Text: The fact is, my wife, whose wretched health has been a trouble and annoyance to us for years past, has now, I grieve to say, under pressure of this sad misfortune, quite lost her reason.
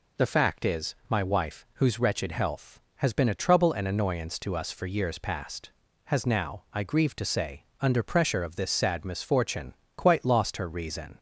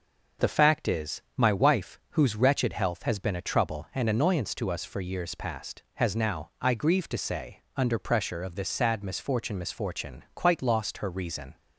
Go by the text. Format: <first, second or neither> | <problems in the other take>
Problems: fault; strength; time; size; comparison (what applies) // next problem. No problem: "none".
first | starts louder than the rest; noticeable; until 1.5 s; 6 dB // says "misfortune" twice; at 9.5 s